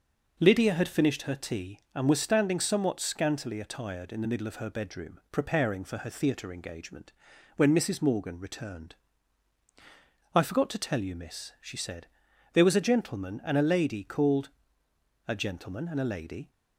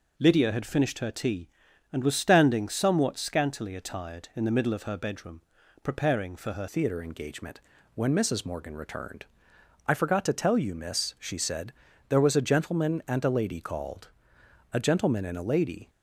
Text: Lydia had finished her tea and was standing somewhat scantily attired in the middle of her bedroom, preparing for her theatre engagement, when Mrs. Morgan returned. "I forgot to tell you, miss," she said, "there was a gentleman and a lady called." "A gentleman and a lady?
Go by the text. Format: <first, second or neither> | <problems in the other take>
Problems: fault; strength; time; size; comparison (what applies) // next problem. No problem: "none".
first | changes voice at "theatre"; from 6.6 s on; 9.2 s long